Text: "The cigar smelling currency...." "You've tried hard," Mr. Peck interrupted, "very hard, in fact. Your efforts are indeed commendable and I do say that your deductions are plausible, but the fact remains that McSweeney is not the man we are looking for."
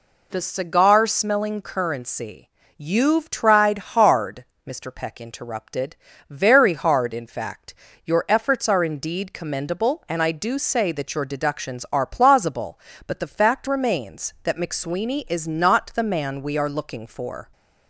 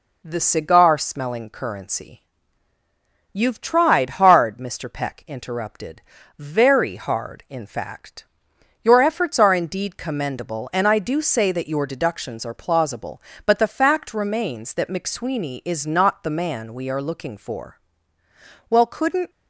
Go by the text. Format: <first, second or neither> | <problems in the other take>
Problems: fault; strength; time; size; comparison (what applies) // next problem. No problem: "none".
first | goes on to say "Well couldn't"; from 18.6 s on; 0.60 s long